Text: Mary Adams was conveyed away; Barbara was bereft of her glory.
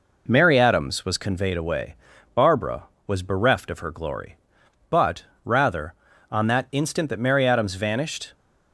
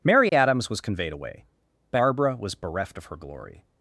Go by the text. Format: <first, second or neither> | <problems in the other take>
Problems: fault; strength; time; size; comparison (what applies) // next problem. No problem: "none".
second | goes on to say "But rather on that instant that Mary Adams vanished"; strong; from 4.8 s on; 3.4 s long